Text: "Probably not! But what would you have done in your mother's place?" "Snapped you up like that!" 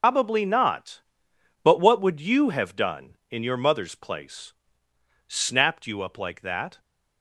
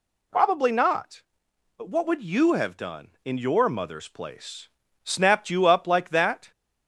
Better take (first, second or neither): second